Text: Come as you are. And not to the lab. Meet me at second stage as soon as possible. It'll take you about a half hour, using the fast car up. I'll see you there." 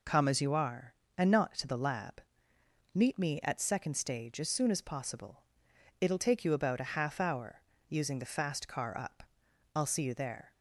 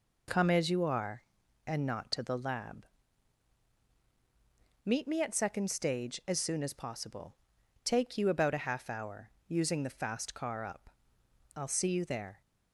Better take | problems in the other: first | skips "It'll"; at 7.5 s

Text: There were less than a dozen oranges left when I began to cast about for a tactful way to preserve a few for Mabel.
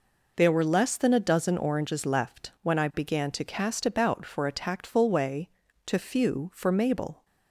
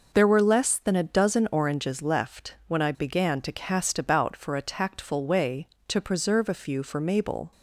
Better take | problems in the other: second | skips "preserve a"; at 5.9 s

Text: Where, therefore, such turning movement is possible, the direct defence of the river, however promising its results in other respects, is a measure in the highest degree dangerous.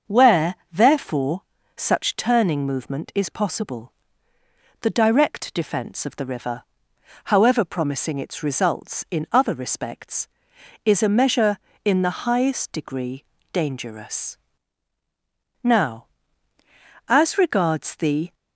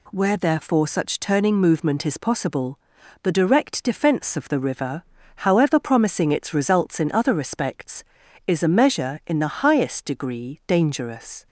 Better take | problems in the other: second | starts louder than the rest; until 1.2 s; 6.5 dB // pauses between "degree" and "dangerous"; slight; at 13.2 s; 0.30 s long // goes on to say "Now as regards the"; strong; from 15.6 s on; 2.7 s long

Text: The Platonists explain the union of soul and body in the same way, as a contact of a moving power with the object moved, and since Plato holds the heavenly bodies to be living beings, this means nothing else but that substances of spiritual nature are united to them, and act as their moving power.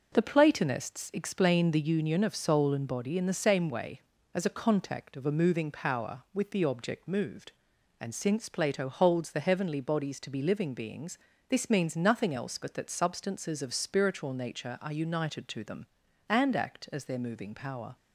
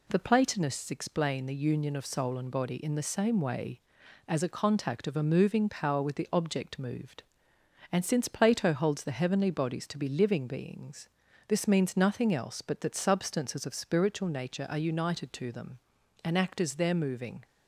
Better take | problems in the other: first | stops before "power"; at 17.4 s

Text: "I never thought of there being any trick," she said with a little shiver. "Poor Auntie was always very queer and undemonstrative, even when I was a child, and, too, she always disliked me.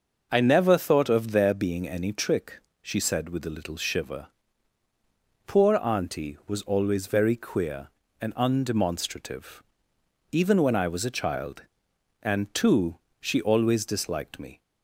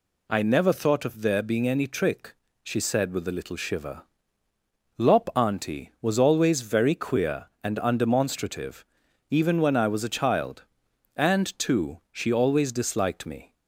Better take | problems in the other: first | says "Lop" for "Poor"; at 4.9 s

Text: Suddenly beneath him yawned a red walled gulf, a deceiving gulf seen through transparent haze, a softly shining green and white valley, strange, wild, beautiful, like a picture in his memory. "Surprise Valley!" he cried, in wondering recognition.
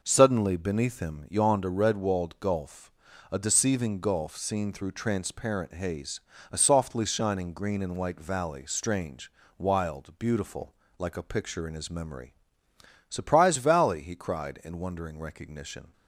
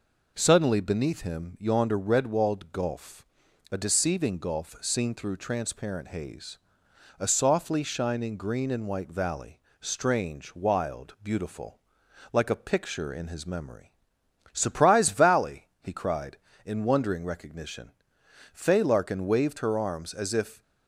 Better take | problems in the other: first | goes on to say "Fay Larkin waved her arms as if"; strong; from 18.5 s on; 2.0 s long

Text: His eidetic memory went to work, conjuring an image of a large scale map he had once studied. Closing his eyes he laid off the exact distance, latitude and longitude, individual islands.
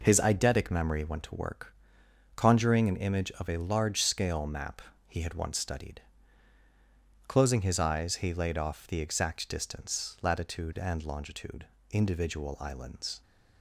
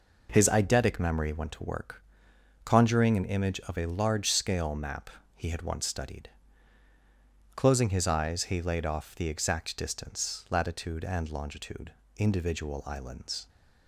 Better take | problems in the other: neither | pauses between "map" and "he"; slight; the same in both

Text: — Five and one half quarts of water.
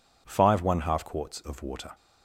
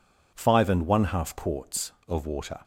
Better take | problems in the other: second | skips "and"; at 0.6 s

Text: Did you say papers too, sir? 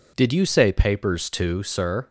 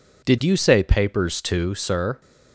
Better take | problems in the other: neither | none

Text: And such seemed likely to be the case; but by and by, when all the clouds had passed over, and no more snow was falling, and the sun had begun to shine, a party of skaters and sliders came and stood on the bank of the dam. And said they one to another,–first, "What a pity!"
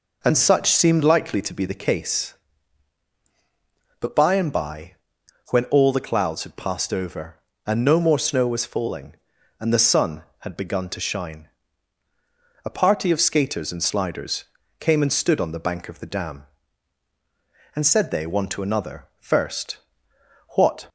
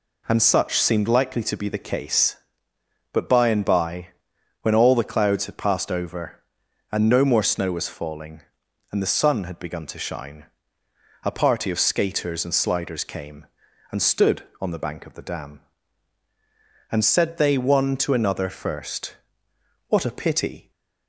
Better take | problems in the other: second | pauses between "sliders" and "came"; slight; at 14.4 s; 0.36 s long // stops before "a pity"; at 20.8 s

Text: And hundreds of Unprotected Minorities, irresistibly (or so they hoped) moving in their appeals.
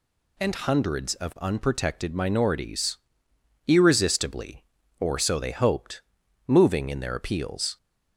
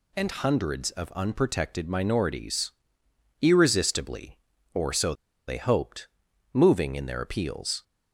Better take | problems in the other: first | pauses between "so" and "they"; slight; at 5.1 s; 0.34 s long

